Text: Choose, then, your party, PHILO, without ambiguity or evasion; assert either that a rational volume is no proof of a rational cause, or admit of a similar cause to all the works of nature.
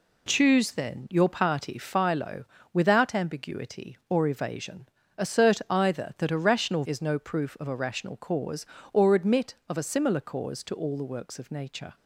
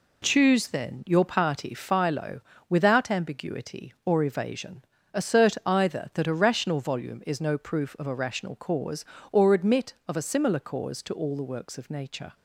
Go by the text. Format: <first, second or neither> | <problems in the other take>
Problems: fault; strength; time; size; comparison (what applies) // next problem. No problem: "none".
second | skips "volume"; at 6.8 s